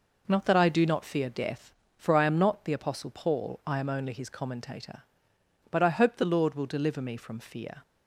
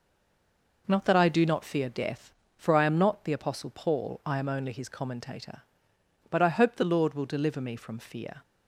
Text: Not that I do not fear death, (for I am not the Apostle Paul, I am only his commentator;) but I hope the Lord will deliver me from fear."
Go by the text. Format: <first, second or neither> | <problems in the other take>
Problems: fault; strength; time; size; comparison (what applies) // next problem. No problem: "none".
first | stays silent before the first word; slight; until 0.8 s; 0.8 s long